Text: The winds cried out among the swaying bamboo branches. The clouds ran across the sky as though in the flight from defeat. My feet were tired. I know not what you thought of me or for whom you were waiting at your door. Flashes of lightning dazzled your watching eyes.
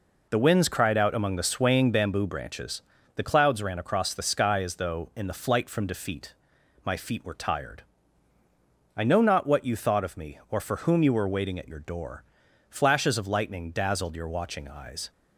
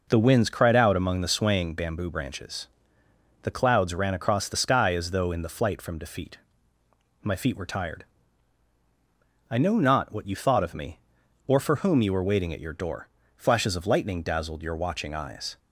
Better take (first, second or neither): neither